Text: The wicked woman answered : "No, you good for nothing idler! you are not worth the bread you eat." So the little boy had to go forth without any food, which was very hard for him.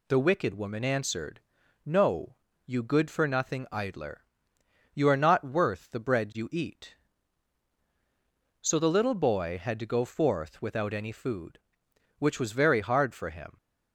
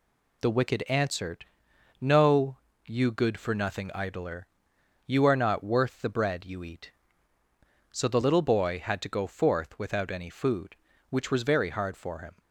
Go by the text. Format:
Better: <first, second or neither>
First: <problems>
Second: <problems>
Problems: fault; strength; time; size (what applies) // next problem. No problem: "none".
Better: first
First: none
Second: skips "woman"; at 0.8 s